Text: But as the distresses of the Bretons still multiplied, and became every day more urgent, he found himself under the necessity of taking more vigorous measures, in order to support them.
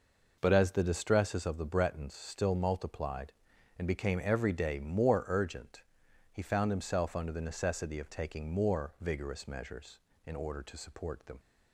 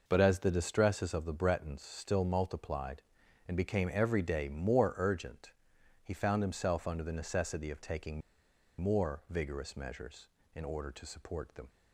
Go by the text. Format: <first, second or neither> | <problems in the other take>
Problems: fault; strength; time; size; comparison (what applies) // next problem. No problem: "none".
first | pauses between "taking" and "more"; noticeable; at 8.2 s; 0.60 s long